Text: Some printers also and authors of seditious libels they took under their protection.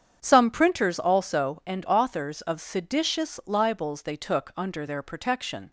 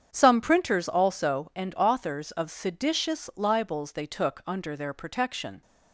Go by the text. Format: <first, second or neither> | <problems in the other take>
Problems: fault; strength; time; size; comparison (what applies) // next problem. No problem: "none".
neither | starts louder than the rest; strong; the same in both